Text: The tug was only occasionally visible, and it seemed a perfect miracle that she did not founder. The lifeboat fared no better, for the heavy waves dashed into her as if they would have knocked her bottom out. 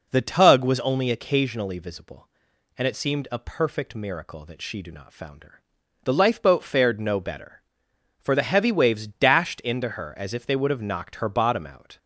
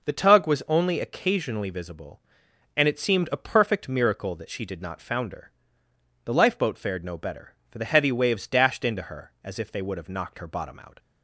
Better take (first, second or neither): second